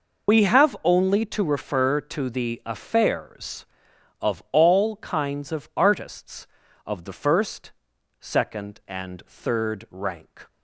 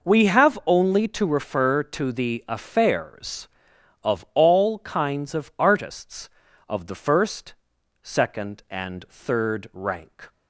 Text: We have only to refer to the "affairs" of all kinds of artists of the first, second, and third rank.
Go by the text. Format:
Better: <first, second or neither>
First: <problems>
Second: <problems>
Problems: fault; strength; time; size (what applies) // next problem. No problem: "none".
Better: second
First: loses the start of "We"; at 0.2 s; 80 ms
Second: none